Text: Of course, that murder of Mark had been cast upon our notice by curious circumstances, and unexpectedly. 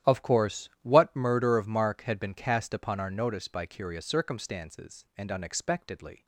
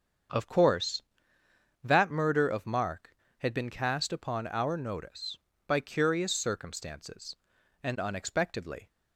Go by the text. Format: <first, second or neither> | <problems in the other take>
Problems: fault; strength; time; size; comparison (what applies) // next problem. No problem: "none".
second | starts louder than the rest; strong; until 1.1 s; 11 dB; strong in the second // says "what" for "that"; at 0.8 s